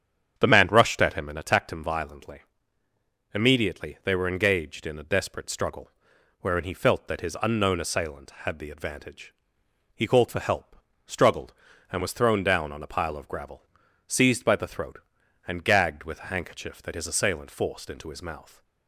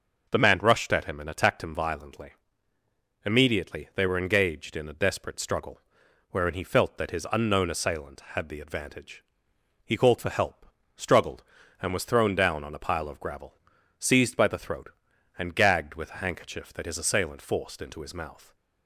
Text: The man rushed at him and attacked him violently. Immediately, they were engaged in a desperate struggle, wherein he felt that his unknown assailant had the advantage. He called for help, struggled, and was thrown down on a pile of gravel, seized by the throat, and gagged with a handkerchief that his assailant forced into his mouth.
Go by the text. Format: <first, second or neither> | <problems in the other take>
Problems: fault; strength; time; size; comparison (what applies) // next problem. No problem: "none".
second | starts louder than the rest; strong; until 1.4 s; 8 dB